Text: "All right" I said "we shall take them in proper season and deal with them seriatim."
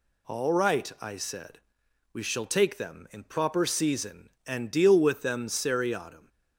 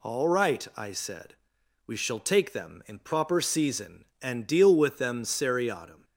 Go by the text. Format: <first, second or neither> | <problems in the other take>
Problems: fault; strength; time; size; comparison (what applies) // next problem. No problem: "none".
neither | pauses between "said" and "we"; noticeable; the same in both